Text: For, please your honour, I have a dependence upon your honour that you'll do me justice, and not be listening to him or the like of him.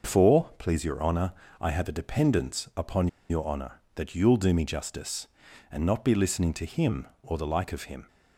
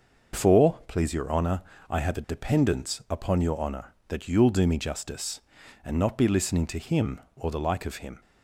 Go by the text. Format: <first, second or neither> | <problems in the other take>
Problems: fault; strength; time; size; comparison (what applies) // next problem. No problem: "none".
second | starts louder than the rest; until 1.1 s; 6 dB; also in the second // pauses between "upon" and "your"; slight; at 3.0 s; 0.22 s long